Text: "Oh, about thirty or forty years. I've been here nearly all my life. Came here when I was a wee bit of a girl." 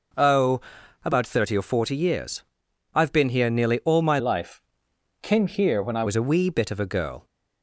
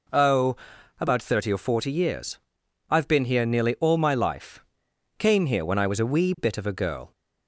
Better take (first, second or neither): second